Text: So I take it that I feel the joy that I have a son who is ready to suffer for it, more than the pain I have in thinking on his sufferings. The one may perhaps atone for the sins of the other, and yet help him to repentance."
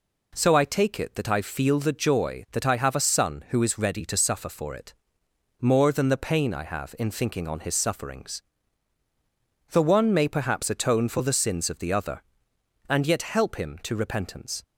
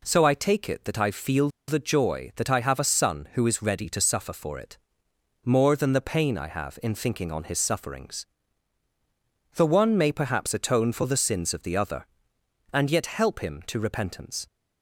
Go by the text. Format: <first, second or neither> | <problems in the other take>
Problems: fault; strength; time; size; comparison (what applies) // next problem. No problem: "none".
first | pauses between "feel" and "the"; slight; at 1.4 s; 0.18 s long